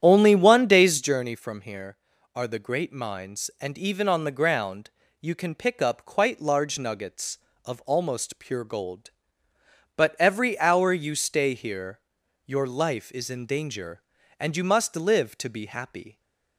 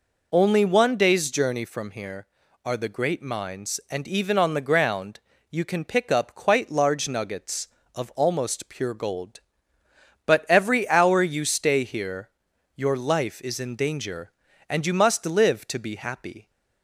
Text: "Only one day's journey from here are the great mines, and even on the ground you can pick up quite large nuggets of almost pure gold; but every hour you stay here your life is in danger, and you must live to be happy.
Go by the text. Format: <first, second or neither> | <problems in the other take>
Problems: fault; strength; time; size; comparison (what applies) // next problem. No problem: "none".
second | starts louder than the rest; strong; until 1.2 s; 10 dB // pauses between "ground" and "you"; slight; at 4.9 s; 0.30 s long; slight in the second // pauses between "here" and "your"; noticeable; at 11.9 s; 0.48 s long; noticeable in the second